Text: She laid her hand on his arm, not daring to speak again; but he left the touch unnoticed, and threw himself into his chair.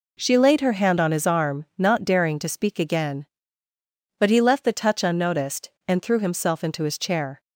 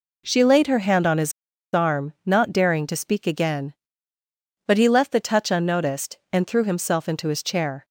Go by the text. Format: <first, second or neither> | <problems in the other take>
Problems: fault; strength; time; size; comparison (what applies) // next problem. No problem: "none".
first | pauses between "his" and "arm"; at 1.3 s; 0.42 s long